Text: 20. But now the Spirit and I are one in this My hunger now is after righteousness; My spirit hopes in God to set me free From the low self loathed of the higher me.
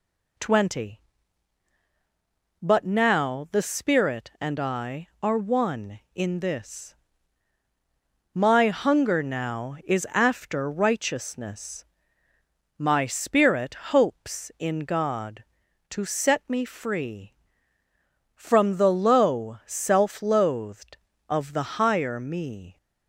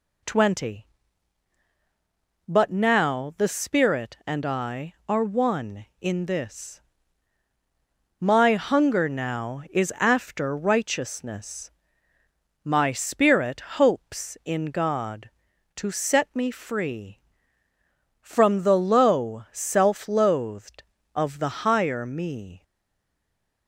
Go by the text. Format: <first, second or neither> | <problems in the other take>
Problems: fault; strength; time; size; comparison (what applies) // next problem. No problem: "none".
first | pauses between "this" and "My"; strong; at 6.8 s; 1.3 s long; strong in the first // stays silent after the last word; from 22.6 s on; 1.0 s long